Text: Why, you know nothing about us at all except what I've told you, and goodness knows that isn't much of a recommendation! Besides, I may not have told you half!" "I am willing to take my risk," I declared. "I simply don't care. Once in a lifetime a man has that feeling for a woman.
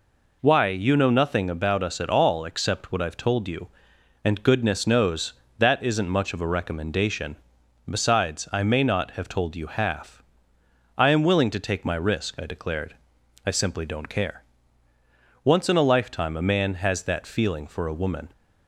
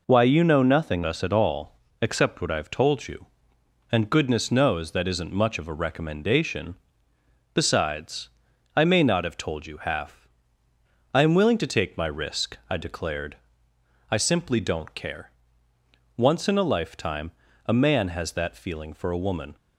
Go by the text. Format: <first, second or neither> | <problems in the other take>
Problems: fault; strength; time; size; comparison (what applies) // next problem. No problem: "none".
first | skips "about"; at 1.0 s // pauses between "all" and "except"; slight; at 1.7 s; 0.24 s long // pauses between "lifetime" and "a"; slight; at 17.3 s; 0.34 s long